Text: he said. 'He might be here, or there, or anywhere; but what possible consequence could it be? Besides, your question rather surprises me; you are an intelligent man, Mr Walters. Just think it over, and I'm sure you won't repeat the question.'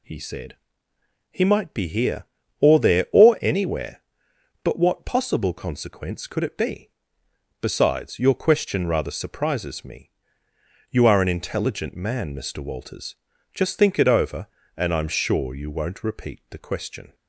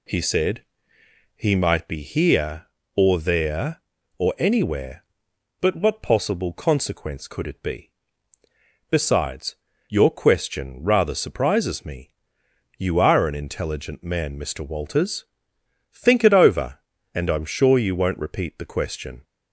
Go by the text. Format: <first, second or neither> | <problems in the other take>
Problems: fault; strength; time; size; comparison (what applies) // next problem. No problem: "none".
first | skips "Just"; at 15.5 s